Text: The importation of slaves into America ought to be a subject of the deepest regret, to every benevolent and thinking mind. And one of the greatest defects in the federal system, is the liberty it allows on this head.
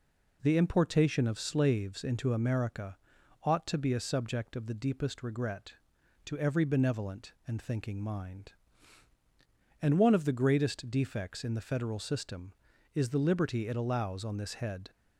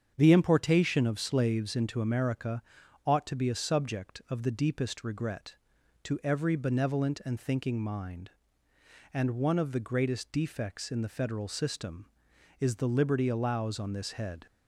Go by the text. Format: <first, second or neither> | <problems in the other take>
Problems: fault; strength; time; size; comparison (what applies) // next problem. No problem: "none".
first | starts louder than the rest; strong; until 1.1 s; 7.5 dB // pauses between "America" and "ought"; at 2.6 s; 0.42 s long; noticeable in the first // skips "it"; at 13.2 s